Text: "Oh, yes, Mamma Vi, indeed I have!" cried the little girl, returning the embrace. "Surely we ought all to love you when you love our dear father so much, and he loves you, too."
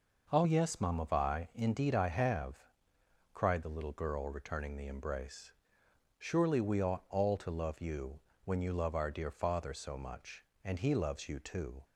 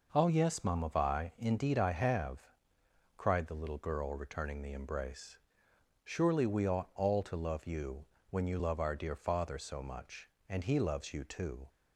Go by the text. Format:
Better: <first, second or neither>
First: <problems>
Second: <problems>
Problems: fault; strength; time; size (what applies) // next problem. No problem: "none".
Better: neither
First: pauses between "you" and "when"; slight; at 8.2 s; 0.22 s long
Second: pauses between "you" and "when"; slight; at 8.0 s; 0.22 s long